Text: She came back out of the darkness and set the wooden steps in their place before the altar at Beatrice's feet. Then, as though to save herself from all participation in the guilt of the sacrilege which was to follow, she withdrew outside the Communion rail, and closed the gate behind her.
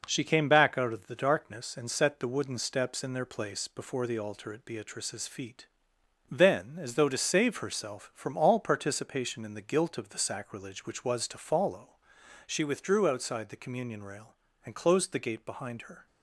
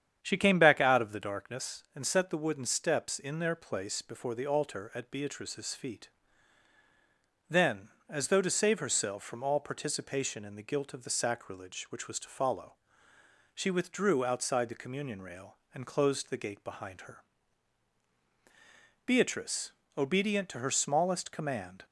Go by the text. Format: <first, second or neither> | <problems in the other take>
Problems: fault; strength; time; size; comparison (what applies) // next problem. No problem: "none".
first | starts louder than the rest; strong; until 1.2 s; 9 dB // goes on to say "Beatrice obedient to her smallest command"; strong; from 19.0 s on; 2.8 s long